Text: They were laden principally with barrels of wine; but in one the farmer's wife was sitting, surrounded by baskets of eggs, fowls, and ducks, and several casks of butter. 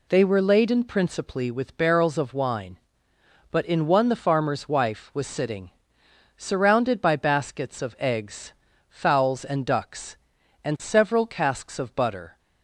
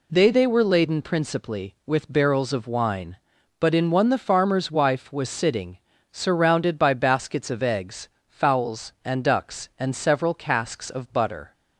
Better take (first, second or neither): first